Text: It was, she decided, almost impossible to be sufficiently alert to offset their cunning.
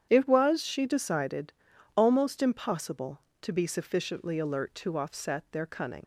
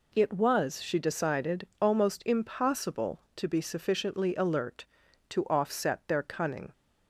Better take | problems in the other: second | starts louder than the rest; strong; until 1.1 s; 8.5 dB // leaves "cunning" unfinished; at 6.0 s; 50 ms

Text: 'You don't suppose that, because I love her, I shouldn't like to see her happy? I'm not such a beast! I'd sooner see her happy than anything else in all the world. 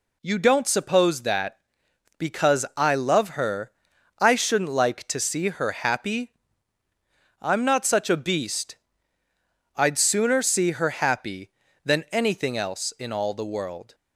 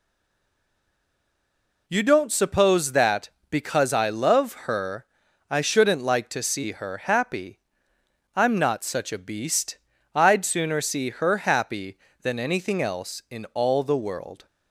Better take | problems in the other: first | stays silent before the first word; noticeable; until 1.8 s; 1.8 s long

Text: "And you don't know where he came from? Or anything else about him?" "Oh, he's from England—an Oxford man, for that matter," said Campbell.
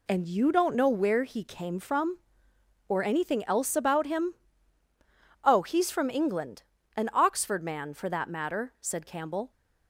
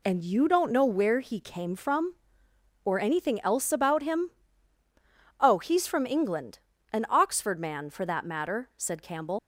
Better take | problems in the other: first | leaves "Campbell" unfinished; at 9.3 s; 75 ms

